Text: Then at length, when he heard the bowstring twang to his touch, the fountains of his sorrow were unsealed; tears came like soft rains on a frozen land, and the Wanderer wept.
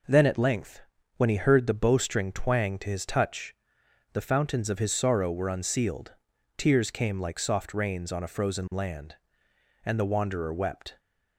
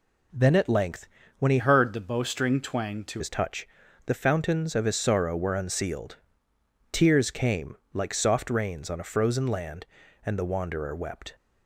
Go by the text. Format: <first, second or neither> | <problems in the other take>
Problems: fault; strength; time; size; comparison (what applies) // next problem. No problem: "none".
first | changes voice from "heard" to "to"; from 1.5 to 3.2 s; 1.7 s long // pauses between "came" and "like"; slight; at 7.7 s; 0.18 s long